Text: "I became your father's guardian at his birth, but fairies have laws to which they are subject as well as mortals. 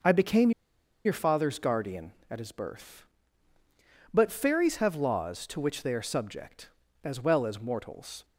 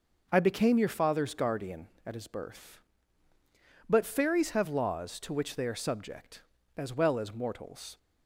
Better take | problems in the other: second | pauses between "became" and "your"; noticeable; at 0.5 s; 0.54 s long

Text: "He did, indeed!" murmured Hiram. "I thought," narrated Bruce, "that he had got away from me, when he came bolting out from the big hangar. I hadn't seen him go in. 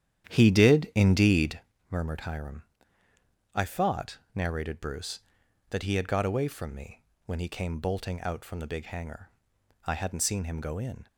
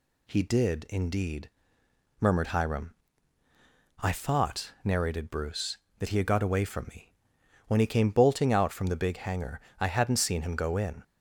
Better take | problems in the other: second | starts louder than the rest; strong; until 1.8 s; 10.5 dB

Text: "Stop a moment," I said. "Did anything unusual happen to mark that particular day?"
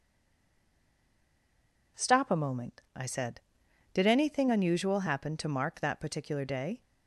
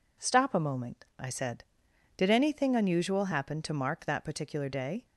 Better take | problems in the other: second | stays silent before the first word; noticeable; until 1.9 s; 1.9 s long

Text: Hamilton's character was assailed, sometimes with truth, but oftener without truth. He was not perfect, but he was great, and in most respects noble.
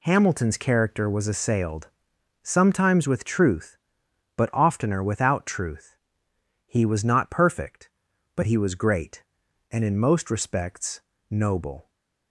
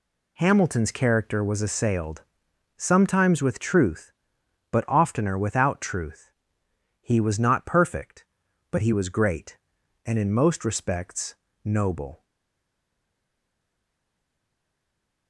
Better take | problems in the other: first | pauses between "respects" and "noble"; slight; at 11.3 s; 0.32 s long; slight in the first // stays silent after the last word; strong; from 12.2 s on; 3.0 s long

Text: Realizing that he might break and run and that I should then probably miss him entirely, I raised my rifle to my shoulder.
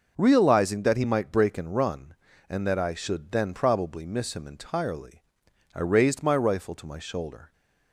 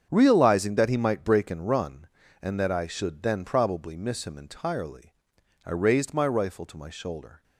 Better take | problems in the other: first | gets quieter; strong; throughout; 12 dB

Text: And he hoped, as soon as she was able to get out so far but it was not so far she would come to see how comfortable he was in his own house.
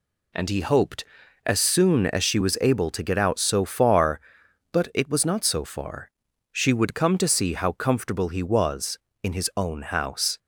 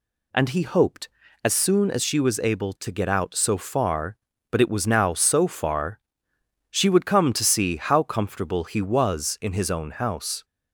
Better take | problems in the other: first | says "now" for "not"; at 4.8 s // pauses between "far" and "she"; noticeable; at 5.9 s; 0.72 s long; also in the first

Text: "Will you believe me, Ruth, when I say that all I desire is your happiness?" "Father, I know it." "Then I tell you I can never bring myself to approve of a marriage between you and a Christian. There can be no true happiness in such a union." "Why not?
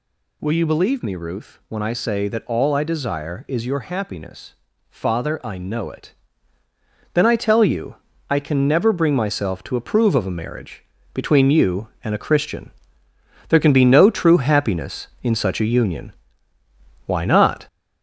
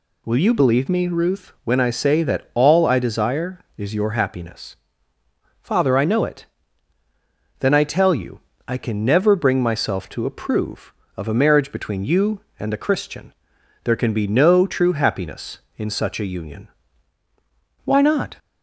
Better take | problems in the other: second | gets louder; noticeable; throughout; 4.5 dB // pauses between "you" and "I"; slight; at 7.9 s; 0.30 s long; slight in the second // pauses between "marriage" and "between"; slight; at 10.8 s; 0.30 s long

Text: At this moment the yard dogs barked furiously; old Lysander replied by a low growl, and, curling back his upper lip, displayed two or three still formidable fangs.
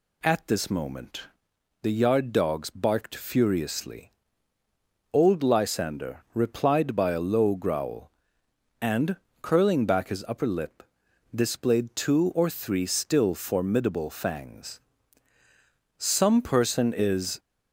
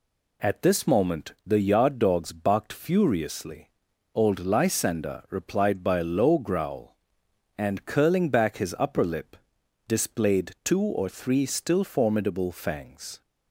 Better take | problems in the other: second | pauses between "moment" and "the"; noticeable; at 1.2 s; 0.60 s long // goes on to say "Some person is"; from 15.9 s on; 1.4 s long

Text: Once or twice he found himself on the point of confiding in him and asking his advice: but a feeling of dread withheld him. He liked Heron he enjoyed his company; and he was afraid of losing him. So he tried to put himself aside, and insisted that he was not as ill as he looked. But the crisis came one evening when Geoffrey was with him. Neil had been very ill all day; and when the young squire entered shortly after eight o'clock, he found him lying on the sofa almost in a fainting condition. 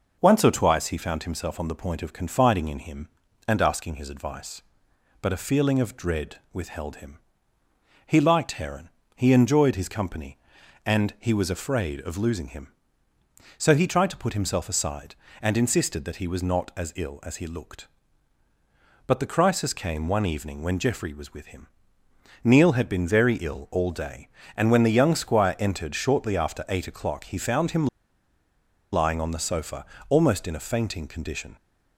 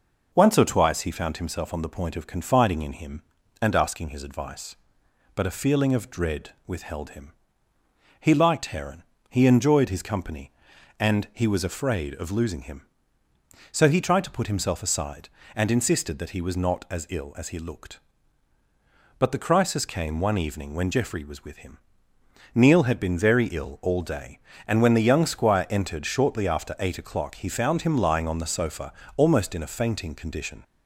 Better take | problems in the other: second | pauses between "dread" and "withheld"; slight; at 6.3 s; 0.18 s long; slight in the second // pauses between "Heron" and "he"; slight; at 8.8 s; 0.26 s long; slight in the second // pauses between "him" and "lying"; at 27.8 s; 1.0 s long // pauses between "sofa" and "almost"; slight; at 29.8 s; 0.24 s long; slight in the second

